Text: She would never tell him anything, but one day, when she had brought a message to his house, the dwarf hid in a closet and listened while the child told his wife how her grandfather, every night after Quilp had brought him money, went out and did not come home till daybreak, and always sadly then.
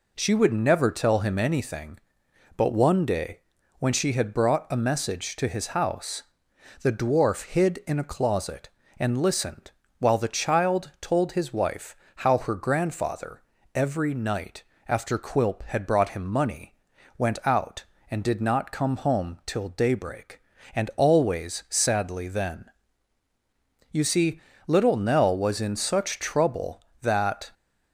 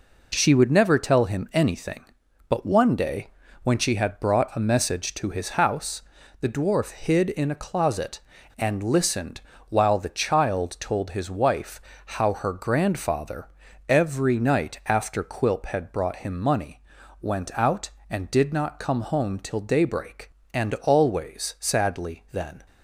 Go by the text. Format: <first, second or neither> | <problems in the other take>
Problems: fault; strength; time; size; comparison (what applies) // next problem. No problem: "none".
second | pauses between "listened" and "while"; slight; at 9.7 s; 0.28 s long; slight in the second // pauses between "wife" and "how"; slight; at 11.9 s; 0.22 s long; slight in the second // pauses between "night" and "after"; slight; at 14.6 s; 0.24 s long // goes on to say "You see little Nell was in such trouble that"; strong; from 23.9 s on; 3.6 s long